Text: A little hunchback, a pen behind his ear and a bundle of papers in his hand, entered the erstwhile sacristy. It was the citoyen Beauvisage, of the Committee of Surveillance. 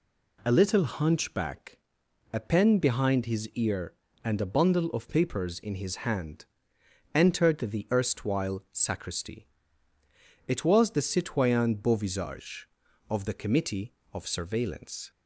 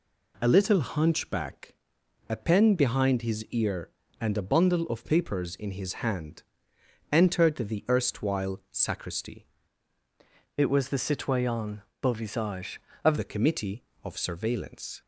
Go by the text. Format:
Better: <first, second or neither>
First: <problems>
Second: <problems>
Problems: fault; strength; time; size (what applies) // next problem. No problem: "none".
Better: first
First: none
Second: changes voice from "It" to "of"; from 10.5 to 13.1 s; 2.6 s long // pauses between "citoyen" and "Beauvisage"; slight; at 11.8 s; 0.20 s long